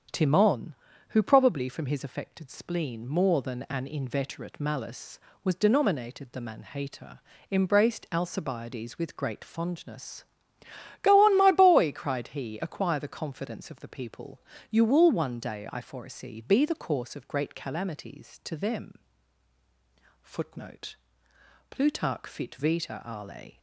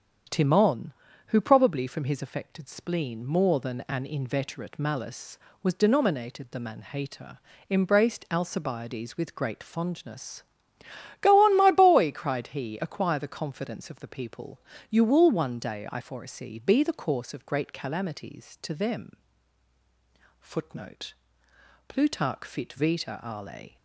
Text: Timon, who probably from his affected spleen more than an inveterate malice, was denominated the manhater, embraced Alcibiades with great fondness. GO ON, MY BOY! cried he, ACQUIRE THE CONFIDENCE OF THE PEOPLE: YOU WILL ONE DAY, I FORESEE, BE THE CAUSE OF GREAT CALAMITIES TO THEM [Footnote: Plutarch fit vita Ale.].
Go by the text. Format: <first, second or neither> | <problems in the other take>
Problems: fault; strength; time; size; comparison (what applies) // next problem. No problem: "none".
neither | starts louder than the rest; strong; the same in both // pauses between "THEM" and "Footnote"; the same in both